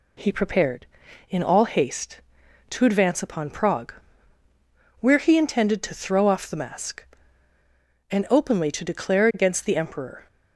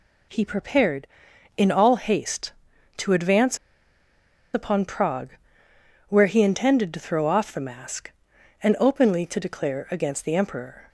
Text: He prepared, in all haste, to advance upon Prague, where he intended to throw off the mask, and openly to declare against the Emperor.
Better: first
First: none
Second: pauses between "advance" and "upon"; noticeable; at 3.5 s; 0.97 s long

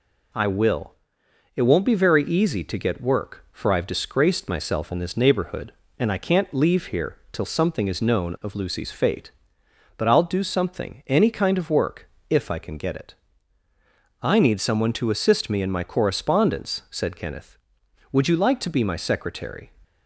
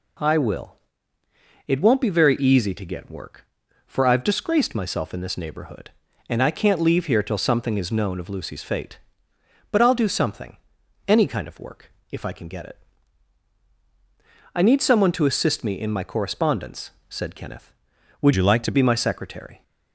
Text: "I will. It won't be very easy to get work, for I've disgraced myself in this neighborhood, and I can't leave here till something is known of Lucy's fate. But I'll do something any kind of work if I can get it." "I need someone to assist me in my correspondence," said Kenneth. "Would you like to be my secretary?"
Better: first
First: pauses between "work" and "if"; slight; at 12.0 s; 0.22 s long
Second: pauses between "something" and "any"; noticeable; at 10.5 s; 0.50 s long // pauses between "work" and "if"; slight; at 11.8 s; 0.20 s long // changes voice from "you" to "to"; from 18.3 to 18.7 s; 0.4 s long

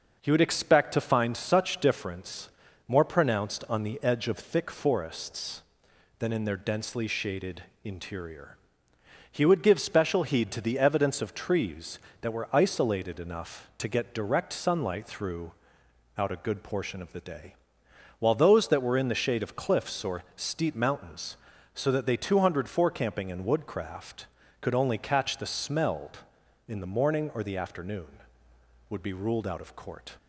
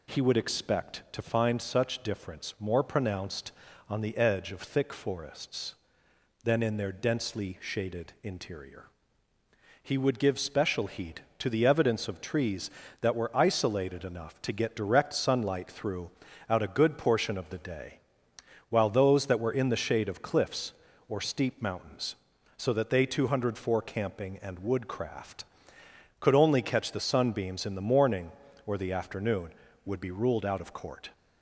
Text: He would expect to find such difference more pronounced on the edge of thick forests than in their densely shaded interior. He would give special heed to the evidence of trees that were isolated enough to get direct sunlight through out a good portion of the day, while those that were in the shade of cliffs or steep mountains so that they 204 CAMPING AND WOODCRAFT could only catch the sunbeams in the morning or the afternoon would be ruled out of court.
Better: second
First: pauses between "difference" and "more"; at 2.4 s; 0.38 s long // pauses between "shaded" and "interior"; slight; at 7.6 s; 0.22 s long // pauses between "through" and "out"; noticeable; at 15.5 s; 0.66 s long // says "smelled" for "sunbeams"; at 25.4 s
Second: pauses between "through" and "out"; at 16.0 s; 0.40 s long

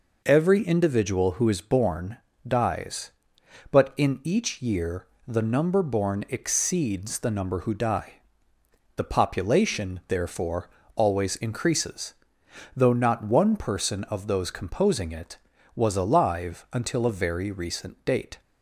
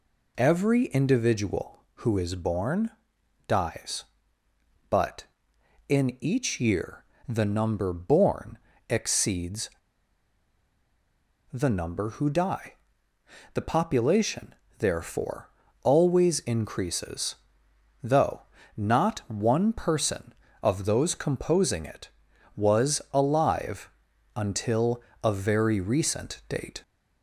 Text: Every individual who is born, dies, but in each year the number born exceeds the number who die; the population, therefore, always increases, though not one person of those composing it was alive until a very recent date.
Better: first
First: pauses between "year" and "the"; slight; at 5.0 s; 0.20 s long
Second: pauses between "year" and "the"; slight; at 7.0 s; 0.24 s long // pauses between "born" and "exceeds"; slight; at 8.5 s; 0.32 s long // pauses between "exceeds" and "the"; strong; at 9.6 s; 1.8 s long // pauses between "though" and "not"; slight; at 18.4 s; 0.34 s long // pauses between "alive" and "until"; at 23.9 s; 0.44 s long // pauses between "until" and "a"; slight; at 25.0 s; 0.20 s long

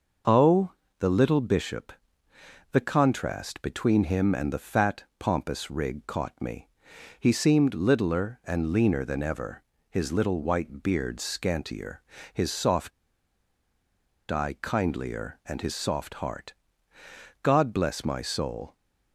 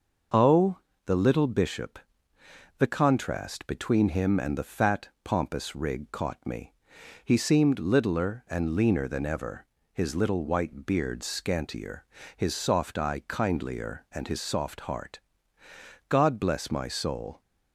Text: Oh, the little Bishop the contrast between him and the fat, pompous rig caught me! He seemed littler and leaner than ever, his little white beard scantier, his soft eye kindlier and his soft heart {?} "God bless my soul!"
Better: second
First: starts louder than the rest; noticeable; until 1.5 s; 6 dB // pauses between "Bishop" and "the"; noticeable; at 1.9 s; 0.80 s long // pauses between "soft" and "eye"; strong; at 12.9 s; 1.3 s long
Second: starts louder than the rest; noticeable; until 1.6 s; 6 dB // pauses between "Bishop" and "the"; noticeable; at 1.9 s; 0.80 s long

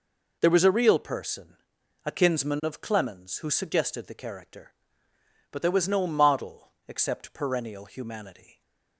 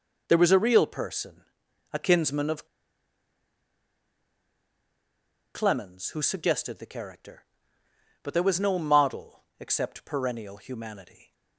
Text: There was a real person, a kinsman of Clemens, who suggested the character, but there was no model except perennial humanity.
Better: first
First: pauses between "model" and "except"; slight; at 6.7 s; 0.16 s long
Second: pauses between "of" and "Clemens"; strong; at 2.6 s; 2.8 s long // pauses between "model" and "except"; slight; at 9.4 s; 0.16 s long

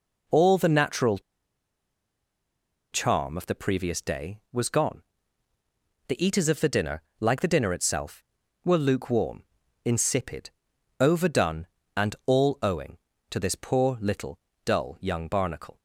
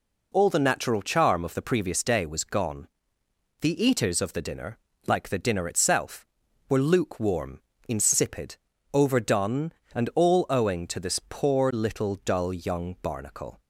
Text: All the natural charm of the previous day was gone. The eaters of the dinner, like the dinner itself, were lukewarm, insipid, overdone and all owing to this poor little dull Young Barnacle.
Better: second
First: pauses between "natural" and "charm"; strong; at 1.1 s; 1.7 s long // pauses between "little" and "dull"; slight; at 14.3 s; 0.28 s long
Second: none

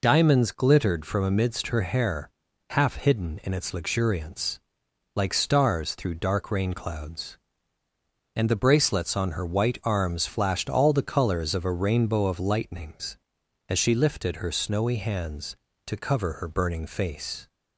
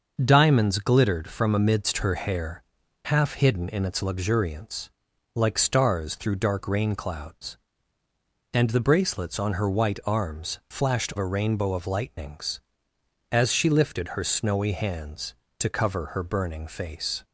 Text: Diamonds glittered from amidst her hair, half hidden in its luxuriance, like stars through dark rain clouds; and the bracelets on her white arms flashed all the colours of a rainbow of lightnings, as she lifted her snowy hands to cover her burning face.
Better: first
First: none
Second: skips "all the colours of"; at 11.1 s

